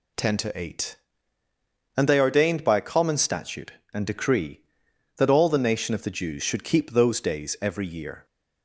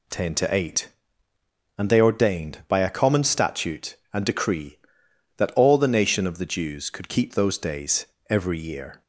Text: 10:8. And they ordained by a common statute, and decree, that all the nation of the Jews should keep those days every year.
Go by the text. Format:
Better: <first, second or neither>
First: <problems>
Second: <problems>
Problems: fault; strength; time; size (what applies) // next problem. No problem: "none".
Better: first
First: none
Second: says "could" for "should"; at 6.8 s // pauses between "days" and "every"; slight; at 8.0 s; 0.24 s long